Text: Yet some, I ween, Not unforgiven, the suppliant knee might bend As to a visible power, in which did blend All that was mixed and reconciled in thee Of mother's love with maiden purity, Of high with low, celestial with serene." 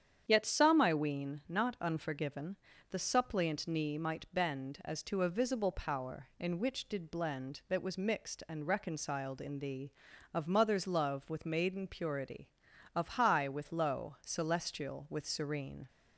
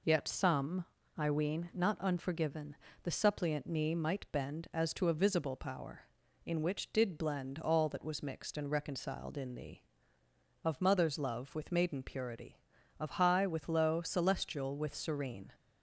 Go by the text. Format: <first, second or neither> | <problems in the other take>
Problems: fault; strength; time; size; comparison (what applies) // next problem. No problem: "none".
second | starts louder than the rest; strong; until 1.2 s; 8.5 dB // skips "All"; at 7.6 s